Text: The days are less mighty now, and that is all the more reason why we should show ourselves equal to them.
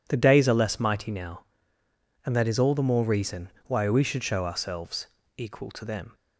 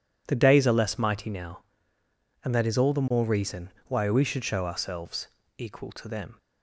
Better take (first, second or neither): neither